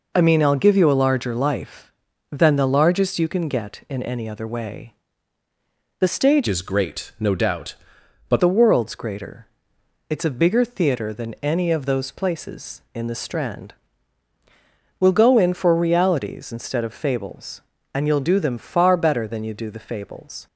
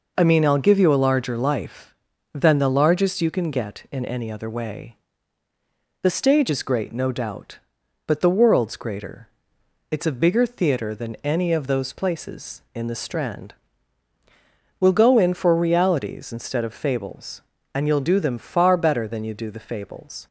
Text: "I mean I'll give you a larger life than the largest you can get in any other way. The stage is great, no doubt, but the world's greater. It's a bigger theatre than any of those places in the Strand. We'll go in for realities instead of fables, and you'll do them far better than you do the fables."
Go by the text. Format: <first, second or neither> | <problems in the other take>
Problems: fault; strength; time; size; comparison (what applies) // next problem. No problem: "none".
second | changes voice from "is" to "but"; from 6.4 to 8.4 s; 2.0 s long